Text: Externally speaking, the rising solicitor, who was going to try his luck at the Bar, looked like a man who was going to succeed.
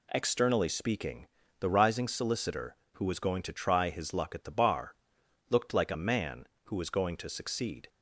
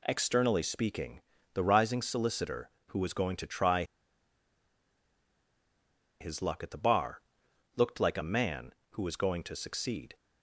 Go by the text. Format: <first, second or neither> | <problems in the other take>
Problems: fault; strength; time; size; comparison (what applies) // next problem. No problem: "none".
first | pauses between "try" and "his"; strong; at 3.8 s; 2.3 s long